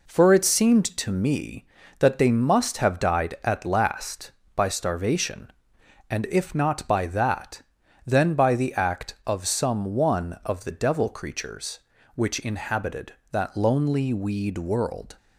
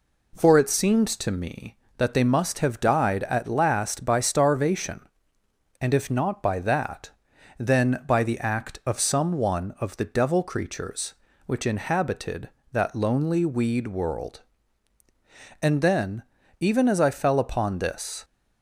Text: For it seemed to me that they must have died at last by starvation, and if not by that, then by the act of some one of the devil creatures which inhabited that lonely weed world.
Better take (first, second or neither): first